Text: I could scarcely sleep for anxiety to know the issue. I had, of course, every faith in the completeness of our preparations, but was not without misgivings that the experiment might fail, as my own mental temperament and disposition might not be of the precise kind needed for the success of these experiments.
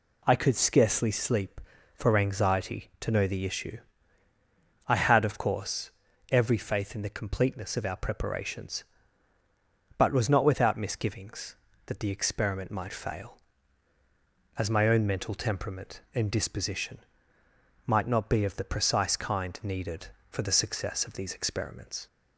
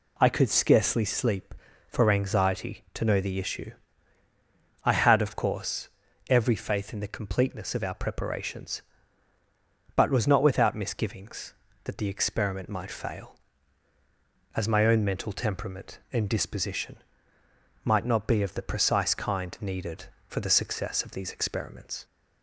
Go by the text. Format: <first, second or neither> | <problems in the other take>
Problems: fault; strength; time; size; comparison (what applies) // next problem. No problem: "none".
neither | pauses between "disposition" and "might"; noticeable; the same in both